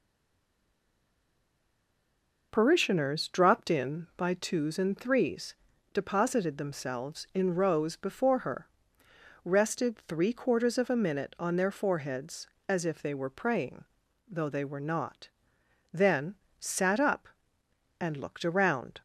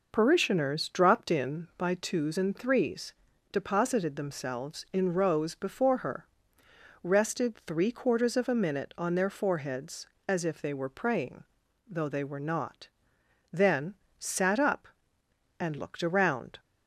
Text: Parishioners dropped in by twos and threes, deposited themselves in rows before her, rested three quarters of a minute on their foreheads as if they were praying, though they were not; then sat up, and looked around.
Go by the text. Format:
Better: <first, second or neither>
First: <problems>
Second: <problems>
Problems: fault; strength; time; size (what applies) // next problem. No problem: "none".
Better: second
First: stays silent before the first word; until 2.5 s; 2.5 s long // pauses between "then" and "sat"; slight; at 16.3 s; 0.26 s long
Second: pauses between "then" and "sat"; slight; at 13.9 s; 0.26 s long